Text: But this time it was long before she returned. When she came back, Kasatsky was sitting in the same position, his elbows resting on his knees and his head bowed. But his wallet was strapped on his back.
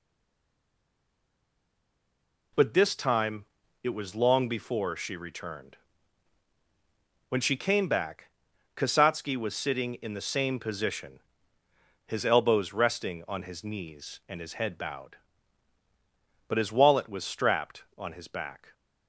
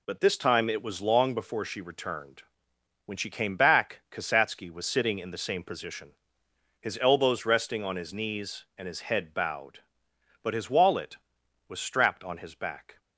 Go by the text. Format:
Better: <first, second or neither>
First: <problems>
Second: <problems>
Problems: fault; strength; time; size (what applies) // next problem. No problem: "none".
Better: second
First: stays silent before the first word; strong; until 2.5 s; 2.5 s long // pauses between "time" and "it"; slight; at 3.4 s; 0.36 s long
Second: none